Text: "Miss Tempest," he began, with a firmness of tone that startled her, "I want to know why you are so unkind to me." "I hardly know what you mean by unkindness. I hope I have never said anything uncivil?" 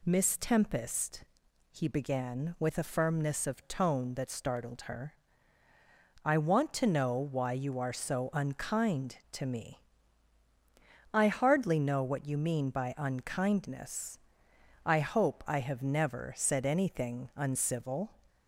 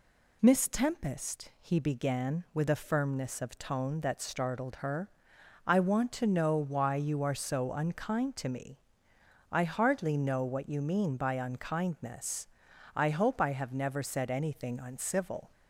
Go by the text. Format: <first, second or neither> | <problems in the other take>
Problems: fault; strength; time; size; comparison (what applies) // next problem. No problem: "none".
neither | none